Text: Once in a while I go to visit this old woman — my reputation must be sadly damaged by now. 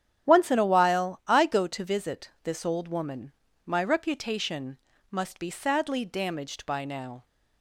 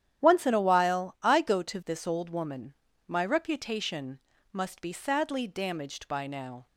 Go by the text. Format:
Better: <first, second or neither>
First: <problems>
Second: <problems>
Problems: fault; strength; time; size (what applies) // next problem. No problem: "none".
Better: first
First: starts louder than the rest; strong; until 1.3 s; 9.5 dB // pauses between "reputation" and "must"; slight; at 4.7 s; 0.32 s long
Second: starts louder than the rest; strong; until 1.2 s; 10.5 dB // skips "visit"; at 1.8 s // pauses between "reputation" and "must"; slight; at 4.2 s; 0.32 s long